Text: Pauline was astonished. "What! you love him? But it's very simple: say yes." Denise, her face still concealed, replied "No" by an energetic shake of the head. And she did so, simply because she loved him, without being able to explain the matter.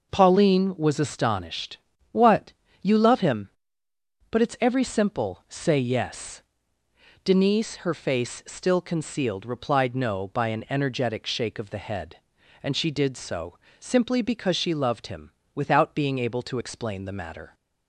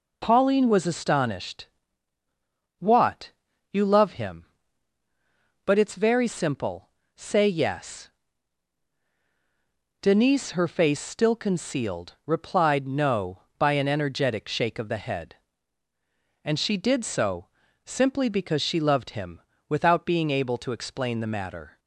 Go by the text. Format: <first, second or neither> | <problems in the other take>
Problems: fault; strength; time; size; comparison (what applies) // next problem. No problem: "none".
second | says "every" for "very"; at 4.6 s